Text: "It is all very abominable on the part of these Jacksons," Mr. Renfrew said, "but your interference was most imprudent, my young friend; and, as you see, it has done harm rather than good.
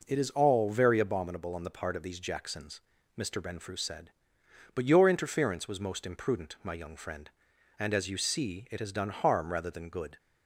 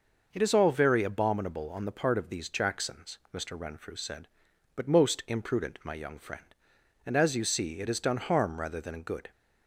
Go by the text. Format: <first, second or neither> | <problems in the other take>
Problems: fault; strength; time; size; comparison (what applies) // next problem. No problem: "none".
first | skips "your interference was"; at 4.8 s